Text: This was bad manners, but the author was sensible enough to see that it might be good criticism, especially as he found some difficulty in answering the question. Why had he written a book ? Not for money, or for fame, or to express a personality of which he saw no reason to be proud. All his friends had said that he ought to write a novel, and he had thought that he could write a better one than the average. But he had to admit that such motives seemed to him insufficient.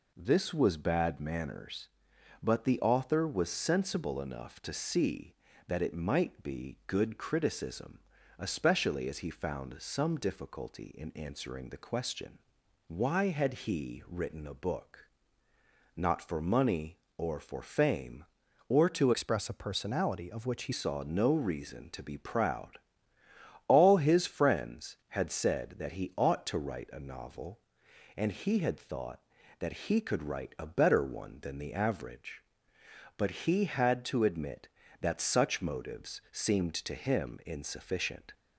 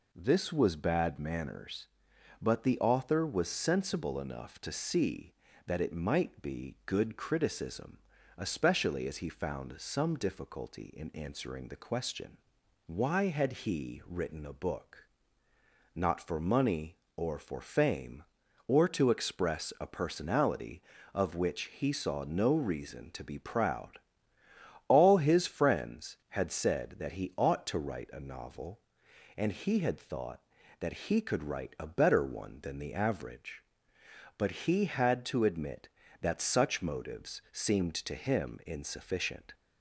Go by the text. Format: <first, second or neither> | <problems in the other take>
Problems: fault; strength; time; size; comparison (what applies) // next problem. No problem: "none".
second | changes voice from "express" to "he"; from 19.1 to 20.7 s; 1.6 s long